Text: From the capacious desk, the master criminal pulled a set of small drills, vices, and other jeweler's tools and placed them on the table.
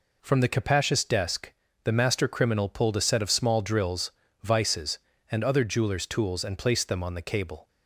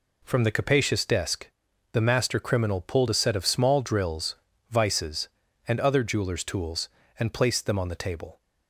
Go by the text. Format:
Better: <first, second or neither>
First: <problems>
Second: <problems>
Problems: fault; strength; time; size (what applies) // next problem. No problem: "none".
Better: second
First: says "cable" for "table"; at 7.2 s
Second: none